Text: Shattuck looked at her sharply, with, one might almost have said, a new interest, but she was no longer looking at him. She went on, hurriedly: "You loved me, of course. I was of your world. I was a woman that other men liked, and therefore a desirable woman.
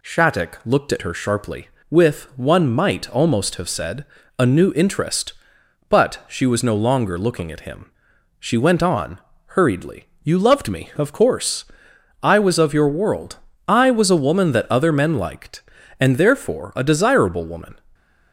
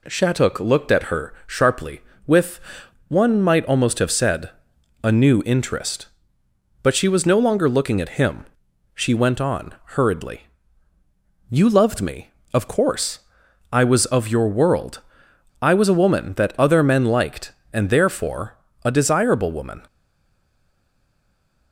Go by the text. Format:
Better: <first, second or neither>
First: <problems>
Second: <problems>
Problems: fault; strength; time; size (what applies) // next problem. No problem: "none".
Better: first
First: none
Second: pauses between "therefore" and "a"; slight; at 18.5 s; 0.28 s long // stays silent after the last word; noticeable; from 19.8 s on; 1.9 s long